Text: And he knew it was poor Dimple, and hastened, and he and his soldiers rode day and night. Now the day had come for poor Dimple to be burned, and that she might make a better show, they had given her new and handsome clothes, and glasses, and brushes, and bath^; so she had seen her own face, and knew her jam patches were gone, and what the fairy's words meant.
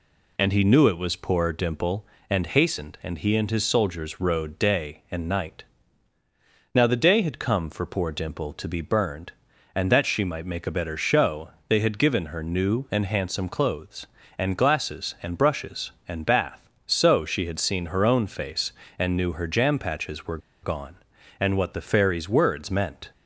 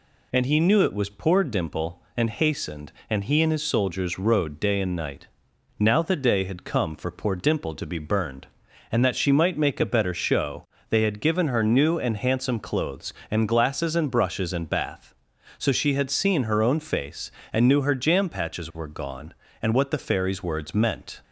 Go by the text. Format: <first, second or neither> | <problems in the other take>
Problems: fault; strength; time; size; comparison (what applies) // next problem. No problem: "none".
second | pauses between "were" and "gone"; slight; at 20.3 s; 0.24 s long